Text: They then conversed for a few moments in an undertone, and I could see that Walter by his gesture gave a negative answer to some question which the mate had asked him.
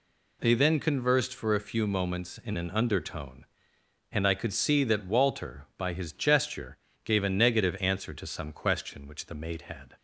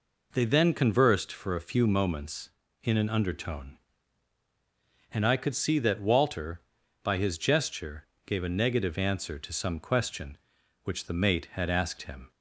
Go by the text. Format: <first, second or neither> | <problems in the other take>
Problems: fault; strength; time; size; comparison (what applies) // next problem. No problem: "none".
second | pauses between "gesture" and "gave"; slight; at 6.7 s; 0.28 s long; slight in the second // stops before "asked him"; at 9.9 s